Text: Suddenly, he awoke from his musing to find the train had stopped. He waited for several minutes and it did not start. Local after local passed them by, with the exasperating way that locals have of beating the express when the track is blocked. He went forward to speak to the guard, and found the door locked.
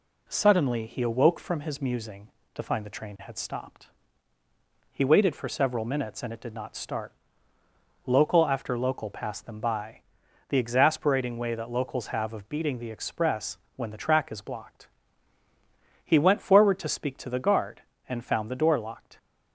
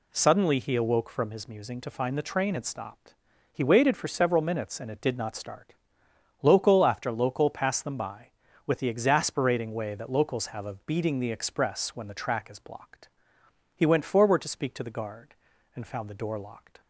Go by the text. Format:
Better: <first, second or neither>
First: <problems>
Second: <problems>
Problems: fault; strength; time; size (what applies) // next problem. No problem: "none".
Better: second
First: skips "with"; at 10.2 s // pauses between "express" and "when"; slight; at 13.5 s; 0.18 s long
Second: none